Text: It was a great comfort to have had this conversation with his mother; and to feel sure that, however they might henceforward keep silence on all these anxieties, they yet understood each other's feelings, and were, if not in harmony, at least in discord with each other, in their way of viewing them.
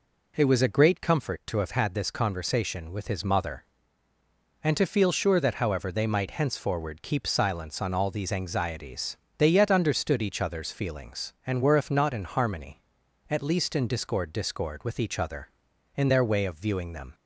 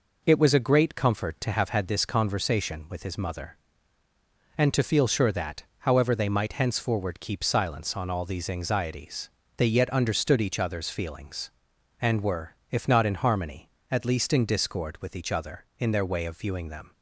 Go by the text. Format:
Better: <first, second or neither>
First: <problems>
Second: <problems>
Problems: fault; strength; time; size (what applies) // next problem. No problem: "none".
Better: second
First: says "discord" twice; at 14.3 s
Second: none